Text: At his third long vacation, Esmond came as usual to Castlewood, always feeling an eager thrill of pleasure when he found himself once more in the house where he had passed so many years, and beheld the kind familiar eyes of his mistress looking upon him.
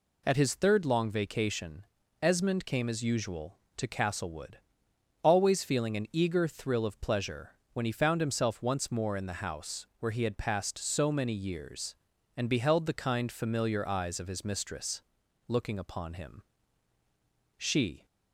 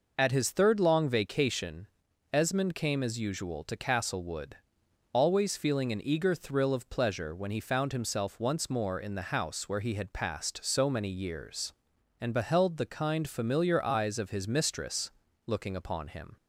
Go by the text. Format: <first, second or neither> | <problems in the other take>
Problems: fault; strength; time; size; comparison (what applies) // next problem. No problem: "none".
second | pauses between "pleasure" and "when"; slight; at 7.5 s; 0.22 s long // pauses between "mistress" and "looking"; noticeable; at 15.0 s; 0.50 s long; slight in the second // goes on to say "She"; slight; from 17.5 s on; 0.48 s long